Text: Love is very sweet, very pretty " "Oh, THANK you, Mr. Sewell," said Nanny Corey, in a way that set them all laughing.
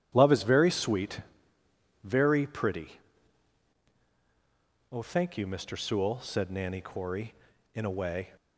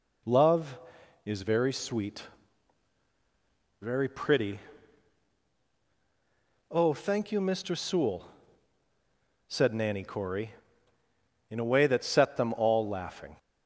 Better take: second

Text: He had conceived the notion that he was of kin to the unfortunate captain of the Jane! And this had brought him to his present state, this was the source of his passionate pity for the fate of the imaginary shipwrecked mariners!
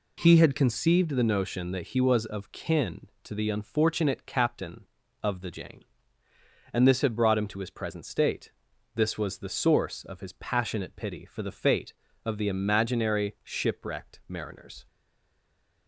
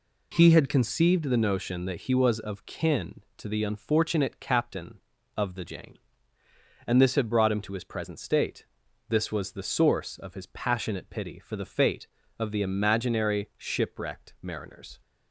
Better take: second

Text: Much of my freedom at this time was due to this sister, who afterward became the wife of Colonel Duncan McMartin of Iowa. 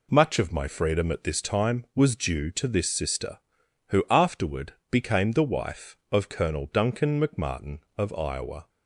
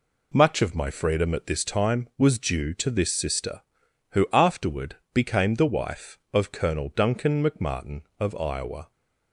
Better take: neither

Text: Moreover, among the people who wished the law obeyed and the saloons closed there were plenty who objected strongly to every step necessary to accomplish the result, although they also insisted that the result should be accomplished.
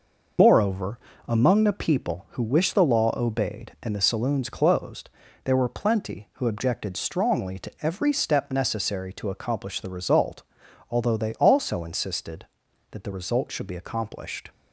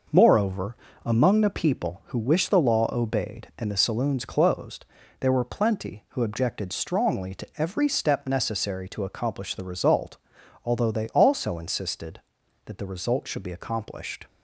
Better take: second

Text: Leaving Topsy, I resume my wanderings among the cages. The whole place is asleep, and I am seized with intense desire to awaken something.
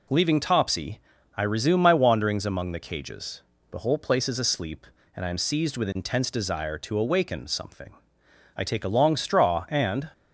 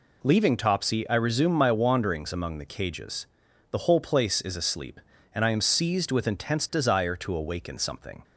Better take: second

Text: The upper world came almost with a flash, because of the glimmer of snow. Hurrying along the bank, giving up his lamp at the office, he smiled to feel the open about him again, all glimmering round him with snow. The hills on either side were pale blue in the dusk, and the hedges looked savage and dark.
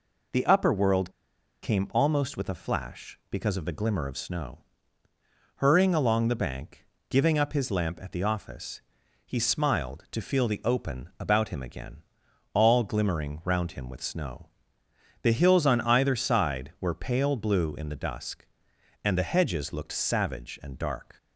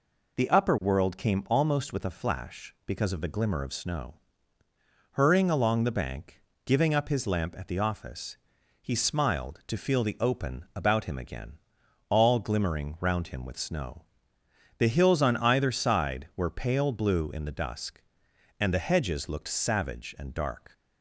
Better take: second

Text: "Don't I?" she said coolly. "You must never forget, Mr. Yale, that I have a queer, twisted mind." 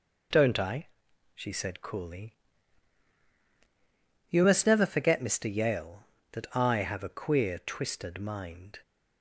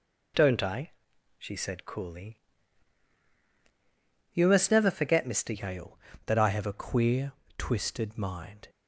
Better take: first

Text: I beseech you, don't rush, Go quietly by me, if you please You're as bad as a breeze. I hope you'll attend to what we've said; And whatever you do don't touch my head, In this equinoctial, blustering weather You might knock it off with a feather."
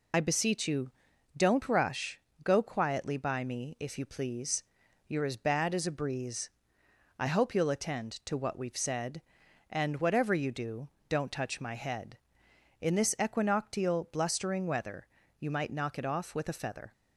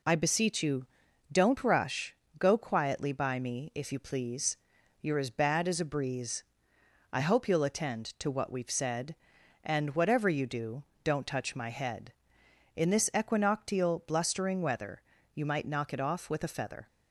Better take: second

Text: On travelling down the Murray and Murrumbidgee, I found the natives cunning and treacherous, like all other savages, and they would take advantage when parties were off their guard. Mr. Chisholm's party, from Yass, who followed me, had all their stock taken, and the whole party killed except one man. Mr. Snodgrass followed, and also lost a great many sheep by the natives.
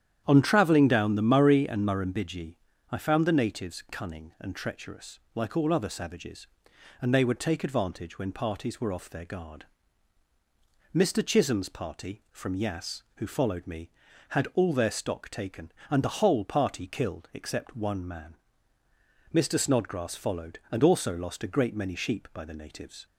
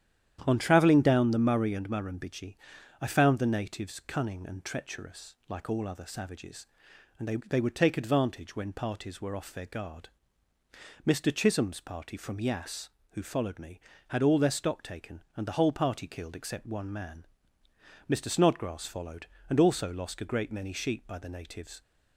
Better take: first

